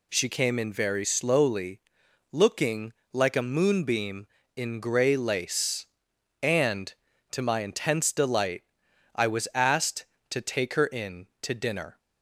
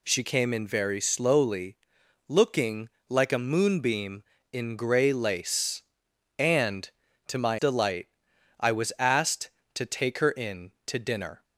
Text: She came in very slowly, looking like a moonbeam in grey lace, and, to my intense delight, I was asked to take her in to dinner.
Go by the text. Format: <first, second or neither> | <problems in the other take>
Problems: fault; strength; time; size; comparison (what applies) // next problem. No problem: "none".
first | pauses between "looking" and "like"; slight; at 2.9 s; 0.18 s long; slight in the first // skips "intense"; at 7.5 s